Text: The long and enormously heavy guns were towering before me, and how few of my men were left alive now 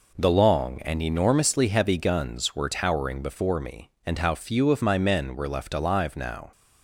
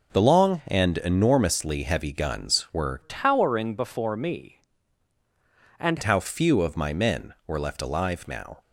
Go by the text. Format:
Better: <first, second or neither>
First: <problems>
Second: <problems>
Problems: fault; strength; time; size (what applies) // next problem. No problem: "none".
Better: first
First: none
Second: changes voice from "towering" to "and"; from 3.0 to 5.9 s; 2.9 s long